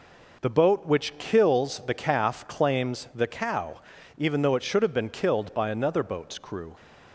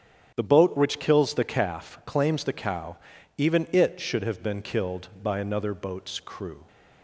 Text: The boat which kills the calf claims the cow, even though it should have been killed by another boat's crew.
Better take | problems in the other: first | starts louder than the rest; strong; until 1.3 s; 9.5 dB // skips "though"; at 3.6 s

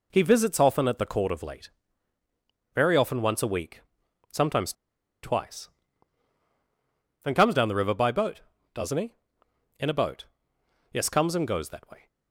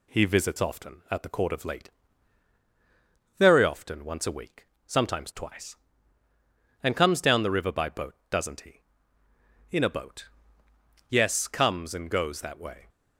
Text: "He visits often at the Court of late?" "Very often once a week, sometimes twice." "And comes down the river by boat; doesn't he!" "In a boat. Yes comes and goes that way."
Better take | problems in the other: second | pauses between "sometimes" and "twice"; noticeable; at 4.7 s; 0.49 s long

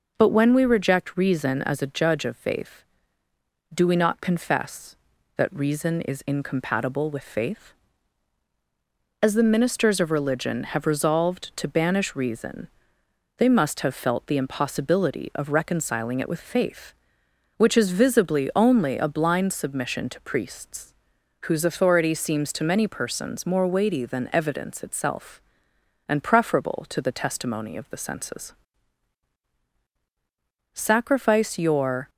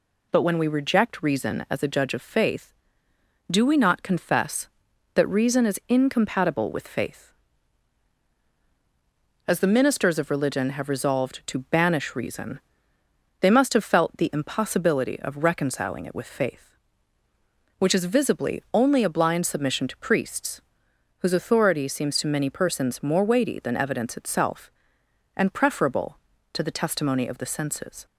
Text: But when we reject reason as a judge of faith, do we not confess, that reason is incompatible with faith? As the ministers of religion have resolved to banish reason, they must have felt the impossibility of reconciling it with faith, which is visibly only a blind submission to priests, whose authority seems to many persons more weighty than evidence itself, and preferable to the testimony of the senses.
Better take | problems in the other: second | goes on to say "Sacrifice your"; from 30.7 s on; 1.3 s long

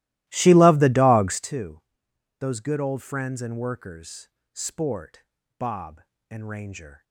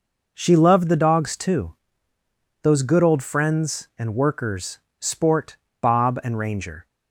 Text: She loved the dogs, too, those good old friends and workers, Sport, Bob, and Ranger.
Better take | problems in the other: second | starts louder than the rest; strong; until 1.5 s; 16.5 dB

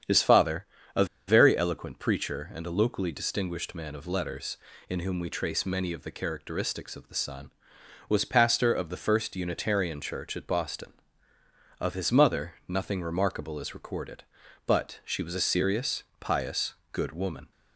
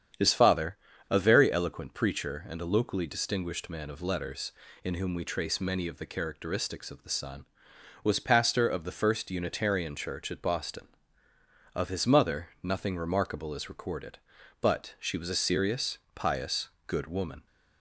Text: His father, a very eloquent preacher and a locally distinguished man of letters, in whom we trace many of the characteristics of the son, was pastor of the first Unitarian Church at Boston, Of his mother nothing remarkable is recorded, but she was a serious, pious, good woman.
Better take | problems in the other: second | starts louder than the rest; strong; until 1.6 s; 8.5 dB; strong in the second // pauses between "a" and "very"; slight; at 1.0 s; 0.22 s long

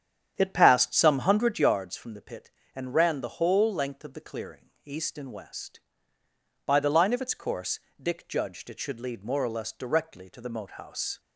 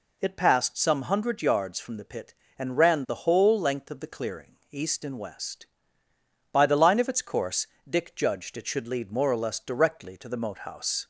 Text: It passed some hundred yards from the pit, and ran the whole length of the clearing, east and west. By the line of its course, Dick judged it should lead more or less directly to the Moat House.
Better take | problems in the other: second | starts louder than the rest; strong; until 1.9 s; 9 dB

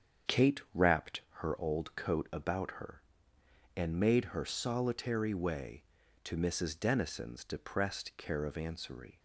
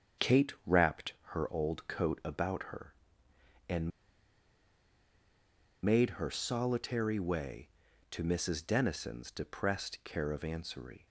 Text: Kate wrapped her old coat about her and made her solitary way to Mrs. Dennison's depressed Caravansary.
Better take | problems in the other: first | starts louder than the rest; strong; until 1.4 s; 7.5 dB; strong in the first // pauses between "wrapped" and "her"; slight; at 1.1 s; 0.18 s long; slight in the first // pauses between "and" and "made"; strong; at 3.9 s; 1.9 s long

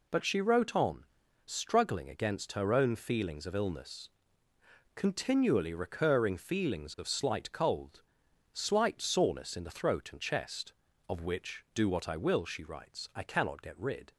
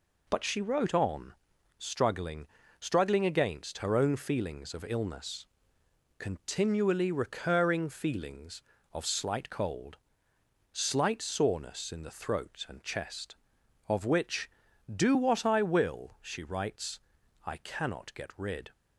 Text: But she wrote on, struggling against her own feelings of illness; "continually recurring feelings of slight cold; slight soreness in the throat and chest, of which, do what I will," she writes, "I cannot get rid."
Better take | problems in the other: first | says "struggling" twice; at 2.7 s

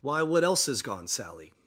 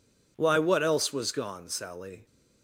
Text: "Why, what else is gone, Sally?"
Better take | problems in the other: first | says "was" for "is"; at 1.1 s

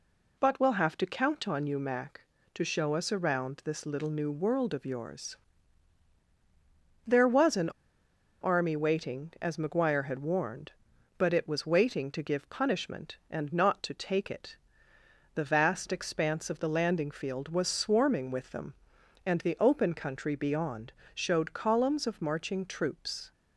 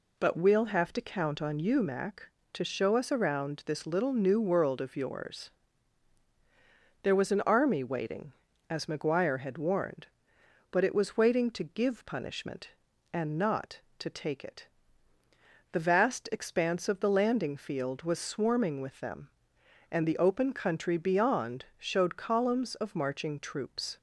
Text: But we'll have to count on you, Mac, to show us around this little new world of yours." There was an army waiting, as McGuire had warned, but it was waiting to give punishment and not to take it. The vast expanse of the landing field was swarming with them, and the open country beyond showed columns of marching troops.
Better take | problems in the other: second | pauses between "an" and "army"; noticeable; at 7.6 s; 0.71 s long // pauses between "beyond" and "showed"; slight; at 20.9 s; 0.22 s long

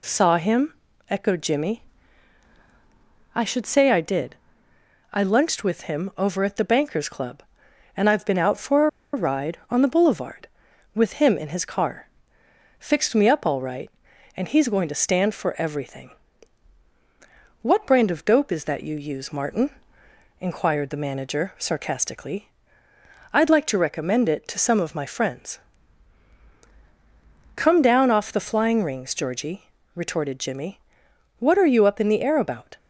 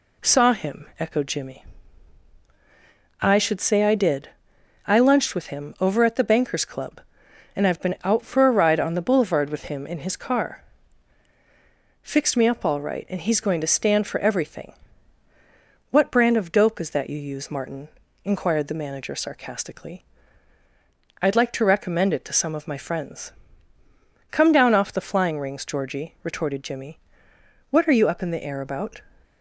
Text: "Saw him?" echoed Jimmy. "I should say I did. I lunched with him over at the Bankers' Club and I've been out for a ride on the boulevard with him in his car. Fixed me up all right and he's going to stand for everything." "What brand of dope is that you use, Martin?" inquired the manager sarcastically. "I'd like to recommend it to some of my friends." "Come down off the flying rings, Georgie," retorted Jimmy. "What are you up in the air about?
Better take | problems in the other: second | pauses between "for" and "a"; slight; at 8.8 s; 0.25 s long

